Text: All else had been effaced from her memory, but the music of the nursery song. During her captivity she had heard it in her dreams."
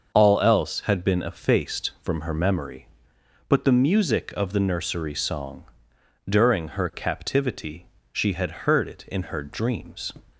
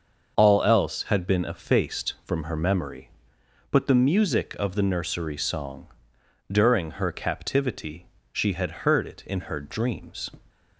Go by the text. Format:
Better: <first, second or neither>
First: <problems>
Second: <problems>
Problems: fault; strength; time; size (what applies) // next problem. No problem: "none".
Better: neither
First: starts louder than the rest; until 1.1 s; 6.5 dB // pauses between "captivity" and "she"; slight; at 7.8 s; 0.26 s long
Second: starts louder than the rest; until 1.3 s; 6.5 dB // pauses between "captivity" and "she"; slight; at 8.0 s; 0.26 s long